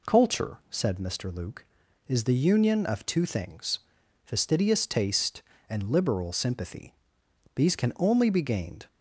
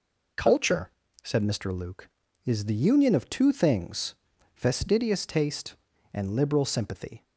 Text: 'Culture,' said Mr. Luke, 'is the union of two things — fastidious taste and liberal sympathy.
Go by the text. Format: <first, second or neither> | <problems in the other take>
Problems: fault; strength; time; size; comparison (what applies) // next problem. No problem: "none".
second | goes on to say "These can only be gained"; from 7.5 s on; 1.3 s long